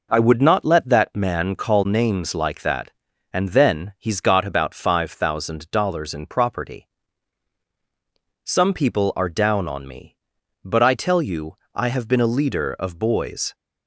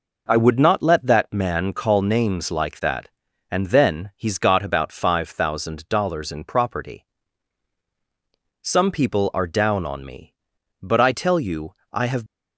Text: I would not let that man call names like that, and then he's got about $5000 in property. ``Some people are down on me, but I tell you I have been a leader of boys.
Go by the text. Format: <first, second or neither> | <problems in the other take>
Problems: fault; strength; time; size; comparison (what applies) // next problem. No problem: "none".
first | pauses between "you" and "I"; slight; at 11.7 s; 0.20 s long; slight in the first // stops before "been a leader of boys"; at 12.2 s